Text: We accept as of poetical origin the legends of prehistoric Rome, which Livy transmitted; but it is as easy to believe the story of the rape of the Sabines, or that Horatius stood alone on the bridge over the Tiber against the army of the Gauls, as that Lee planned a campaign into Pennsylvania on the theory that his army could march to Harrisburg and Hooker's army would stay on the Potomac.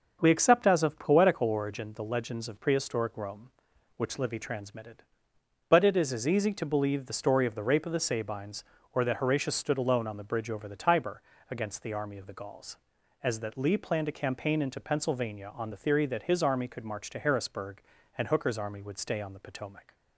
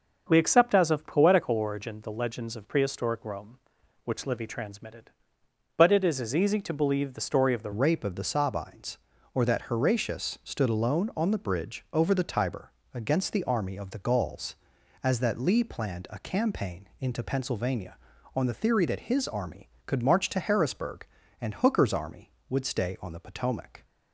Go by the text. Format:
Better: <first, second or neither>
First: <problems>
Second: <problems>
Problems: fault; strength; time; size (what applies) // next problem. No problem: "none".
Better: first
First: starts louder than the rest; until 1.2 s; 6.5 dB // pauses between "Tiber" and "against"; slight; at 11.2 s; 0.28 s long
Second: starts louder than the rest; until 1.3 s; 6.5 dB // changes voice at "rape"; from 7.7 s on; 16.1 s long // pauses between "Tiber" and "against"; slight; at 12.7 s; 0.20 s long